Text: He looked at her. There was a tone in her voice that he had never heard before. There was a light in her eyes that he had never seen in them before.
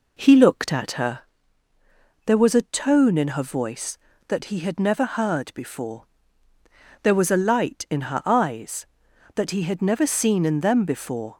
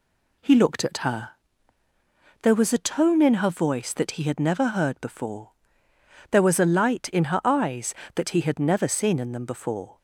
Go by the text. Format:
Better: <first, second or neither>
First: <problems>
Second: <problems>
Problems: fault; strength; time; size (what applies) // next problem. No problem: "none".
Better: second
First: starts louder than the rest; noticeable; until 1.5 s; 4 dB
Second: none